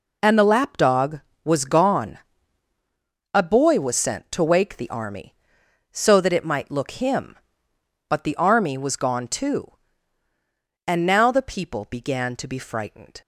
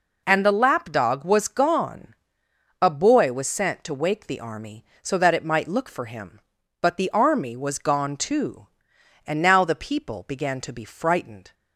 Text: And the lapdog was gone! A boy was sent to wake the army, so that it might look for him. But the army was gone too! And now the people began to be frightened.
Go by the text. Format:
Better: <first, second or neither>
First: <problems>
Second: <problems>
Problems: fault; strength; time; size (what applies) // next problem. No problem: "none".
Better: second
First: skips "for"; at 6.9 s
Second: none